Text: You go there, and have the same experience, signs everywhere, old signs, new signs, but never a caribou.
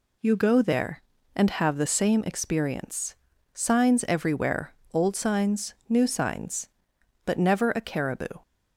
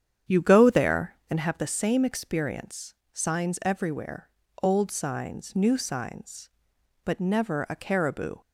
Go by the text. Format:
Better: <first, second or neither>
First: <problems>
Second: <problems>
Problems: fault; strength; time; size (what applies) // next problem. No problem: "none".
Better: first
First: none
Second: starts louder than the rest; strong; until 1.5 s; 8.5 dB